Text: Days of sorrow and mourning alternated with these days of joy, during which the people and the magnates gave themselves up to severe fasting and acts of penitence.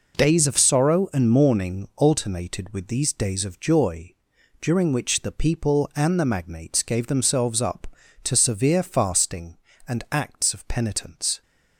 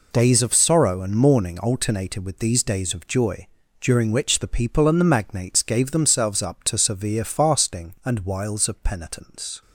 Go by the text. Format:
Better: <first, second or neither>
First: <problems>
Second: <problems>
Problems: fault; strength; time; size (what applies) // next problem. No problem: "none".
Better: first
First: none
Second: says "wiles" for "acts"; at 8.2 s